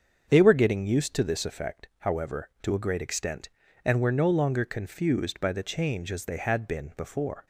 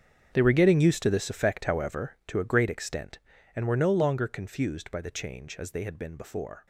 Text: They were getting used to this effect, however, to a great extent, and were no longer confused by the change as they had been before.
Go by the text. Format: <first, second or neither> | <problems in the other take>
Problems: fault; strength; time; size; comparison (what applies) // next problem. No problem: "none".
first | gets quieter; strong; throughout; 16 dB // starts louder than the rest; strong; until 1.3 s; 8 dB; also in the first